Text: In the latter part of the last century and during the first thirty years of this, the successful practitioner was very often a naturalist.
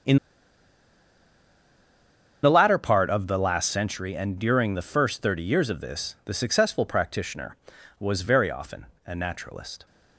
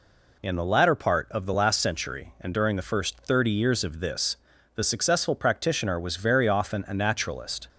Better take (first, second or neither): second